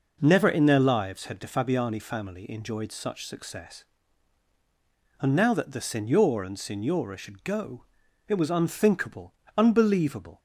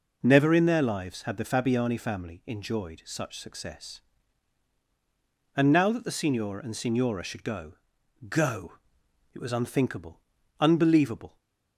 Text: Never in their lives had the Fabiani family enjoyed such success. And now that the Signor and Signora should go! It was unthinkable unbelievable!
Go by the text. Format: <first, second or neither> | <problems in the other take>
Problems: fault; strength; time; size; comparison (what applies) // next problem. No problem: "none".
first | says "go" twice; at 8.2 s // pauses between "unthinkable" and "unbelievable"; at 10.2 s; 0.40 s long; slight in the first